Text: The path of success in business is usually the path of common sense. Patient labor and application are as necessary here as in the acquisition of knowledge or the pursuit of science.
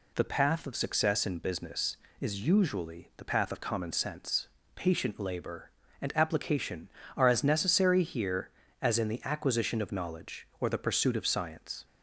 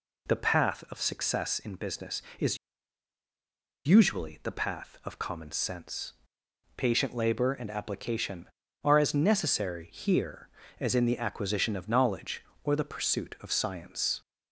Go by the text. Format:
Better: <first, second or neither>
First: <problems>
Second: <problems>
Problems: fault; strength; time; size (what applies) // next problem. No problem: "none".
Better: first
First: none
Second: pauses between "is" and "usually"; strong; at 2.5 s; 1.2 s long